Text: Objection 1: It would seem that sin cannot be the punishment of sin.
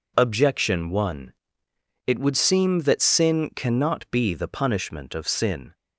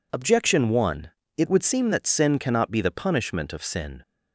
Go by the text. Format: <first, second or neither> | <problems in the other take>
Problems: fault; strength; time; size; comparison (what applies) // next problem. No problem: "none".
neither | none